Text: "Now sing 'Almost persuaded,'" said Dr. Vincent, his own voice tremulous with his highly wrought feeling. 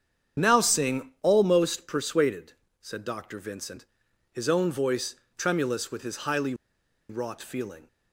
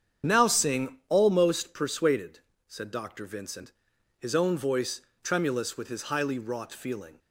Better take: second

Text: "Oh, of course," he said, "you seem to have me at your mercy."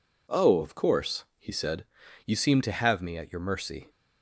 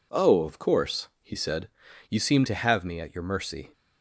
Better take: neither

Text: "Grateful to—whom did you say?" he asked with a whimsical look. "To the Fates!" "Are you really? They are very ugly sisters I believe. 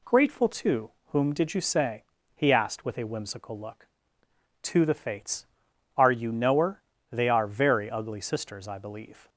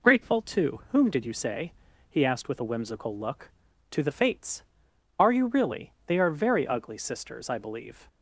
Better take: second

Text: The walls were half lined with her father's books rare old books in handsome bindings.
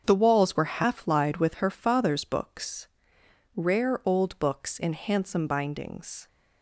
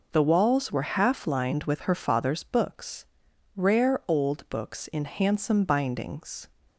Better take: second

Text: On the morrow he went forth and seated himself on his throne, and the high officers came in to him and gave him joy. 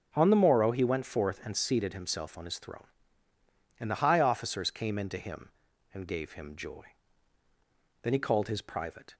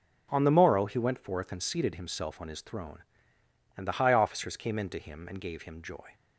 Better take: second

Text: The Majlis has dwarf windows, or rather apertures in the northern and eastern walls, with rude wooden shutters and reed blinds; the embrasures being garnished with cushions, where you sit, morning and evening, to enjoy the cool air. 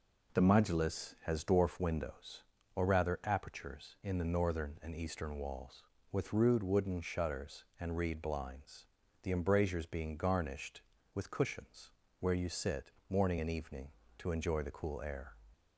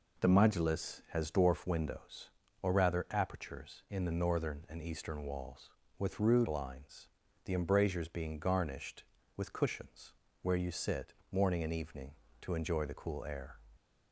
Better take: first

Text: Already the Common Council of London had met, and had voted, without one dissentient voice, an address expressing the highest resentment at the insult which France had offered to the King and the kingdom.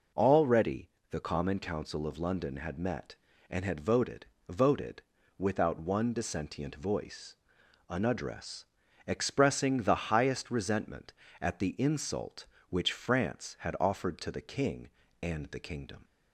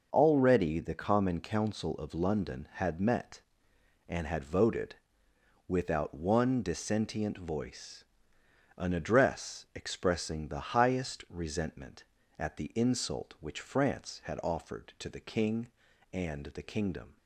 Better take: second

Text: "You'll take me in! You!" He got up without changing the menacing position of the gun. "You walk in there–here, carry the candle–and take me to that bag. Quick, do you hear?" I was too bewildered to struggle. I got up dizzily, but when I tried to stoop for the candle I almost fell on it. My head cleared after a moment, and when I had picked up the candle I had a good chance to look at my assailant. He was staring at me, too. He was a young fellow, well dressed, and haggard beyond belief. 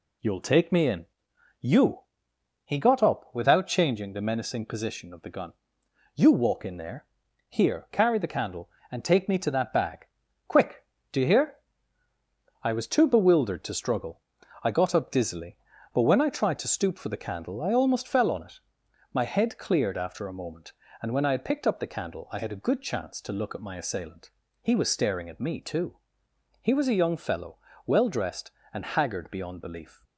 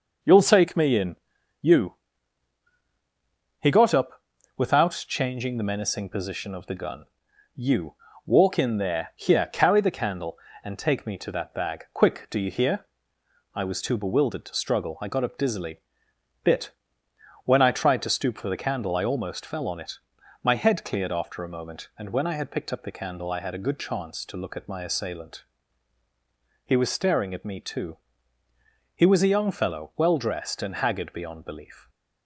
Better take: first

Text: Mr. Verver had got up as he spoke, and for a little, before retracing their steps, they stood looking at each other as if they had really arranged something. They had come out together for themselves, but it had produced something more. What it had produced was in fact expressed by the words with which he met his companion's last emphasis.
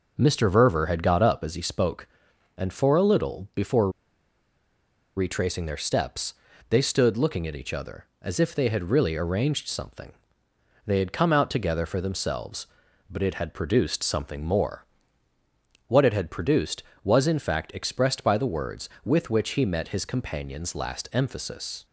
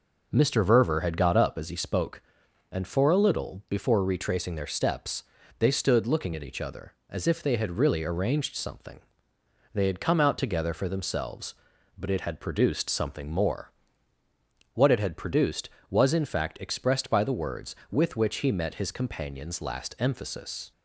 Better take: second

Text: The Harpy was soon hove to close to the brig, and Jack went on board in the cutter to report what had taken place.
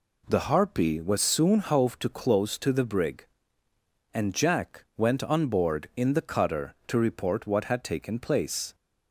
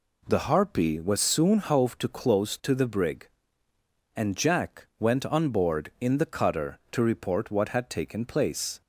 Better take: neither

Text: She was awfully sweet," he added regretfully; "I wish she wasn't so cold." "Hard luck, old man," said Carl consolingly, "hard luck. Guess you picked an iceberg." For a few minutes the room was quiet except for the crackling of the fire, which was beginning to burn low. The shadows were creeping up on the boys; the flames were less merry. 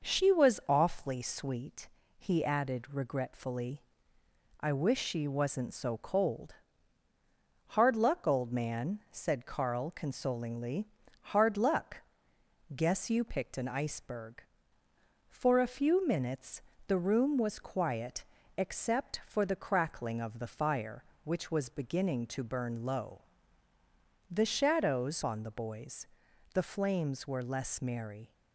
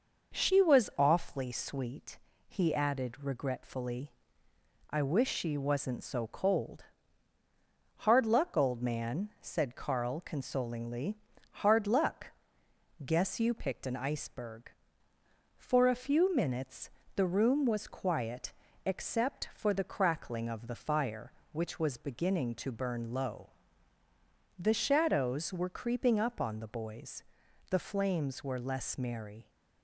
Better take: second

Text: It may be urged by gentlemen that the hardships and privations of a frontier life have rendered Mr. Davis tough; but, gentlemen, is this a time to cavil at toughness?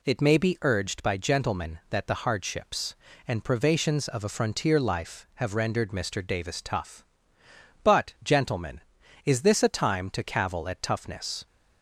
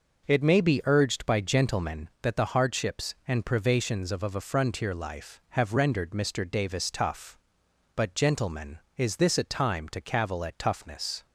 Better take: first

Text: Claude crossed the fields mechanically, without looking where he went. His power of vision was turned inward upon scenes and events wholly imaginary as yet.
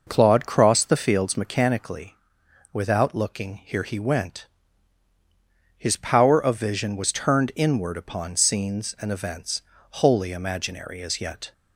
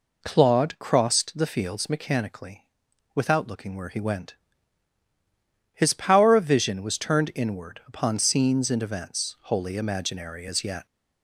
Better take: second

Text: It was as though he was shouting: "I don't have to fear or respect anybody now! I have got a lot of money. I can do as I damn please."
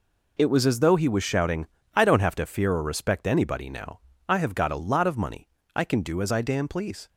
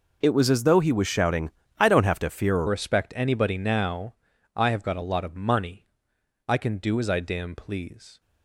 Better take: first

